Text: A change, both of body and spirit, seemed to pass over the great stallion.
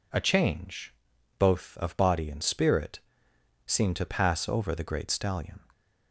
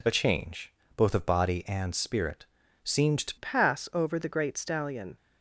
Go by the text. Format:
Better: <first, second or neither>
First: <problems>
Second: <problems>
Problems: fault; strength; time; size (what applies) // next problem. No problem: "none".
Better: first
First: none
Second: changes voice at "pass"; from 3.3 s on; 1.8 s long